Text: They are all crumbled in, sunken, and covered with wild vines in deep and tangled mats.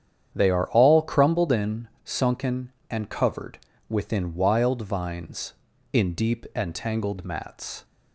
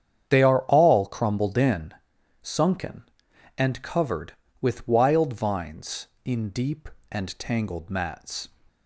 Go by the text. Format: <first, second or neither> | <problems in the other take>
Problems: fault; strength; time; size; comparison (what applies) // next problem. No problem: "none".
second | starts louder than the rest; strong; until 1.3 s; 9 dB; strong in the second // says "within" for "with"; at 3.8 s